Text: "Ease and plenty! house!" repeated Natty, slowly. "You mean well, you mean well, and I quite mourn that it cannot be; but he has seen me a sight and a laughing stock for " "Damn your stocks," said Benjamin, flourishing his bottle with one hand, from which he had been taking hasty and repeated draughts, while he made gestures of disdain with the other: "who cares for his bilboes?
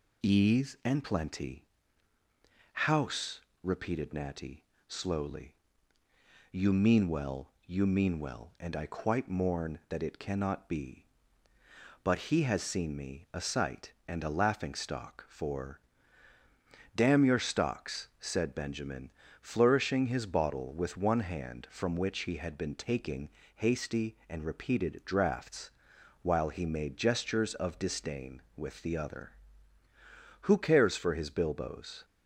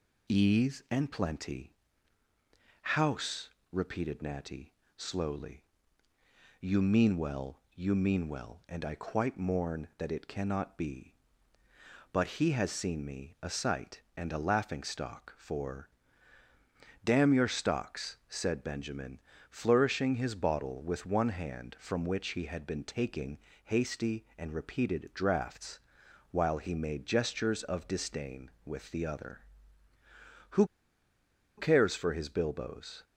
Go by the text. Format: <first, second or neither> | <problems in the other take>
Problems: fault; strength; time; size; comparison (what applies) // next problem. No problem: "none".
first | pauses between "taking" and "hasty"; slight; at 23.3 s; 0.26 s long; slight in the first // pauses between "who" and "cares"; noticeable; at 30.6 s; 0.92 s long